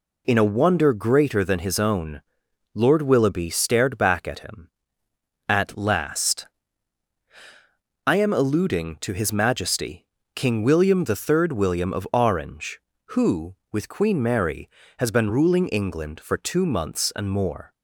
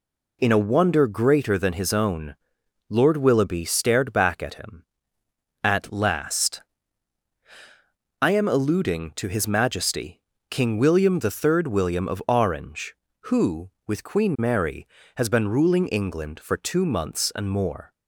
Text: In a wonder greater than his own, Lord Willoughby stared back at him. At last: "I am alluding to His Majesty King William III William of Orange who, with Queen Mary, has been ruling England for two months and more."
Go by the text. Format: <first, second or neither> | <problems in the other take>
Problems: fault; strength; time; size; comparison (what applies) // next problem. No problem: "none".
neither | pauses between "Majesty" and "King"; slight; the same in both